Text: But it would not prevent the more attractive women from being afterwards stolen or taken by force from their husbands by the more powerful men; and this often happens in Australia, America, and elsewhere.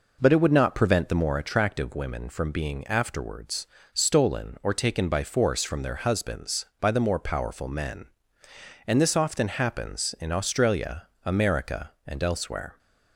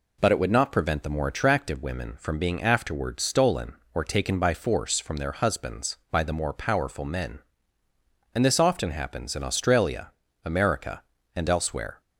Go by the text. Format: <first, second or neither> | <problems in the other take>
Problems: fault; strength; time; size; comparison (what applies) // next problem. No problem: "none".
second | starts louder than the rest; noticeable; until 1.4 s; 5 dB // pauses between "afterwards" and "stolen"; slight; at 3.6 s; 0.26 s long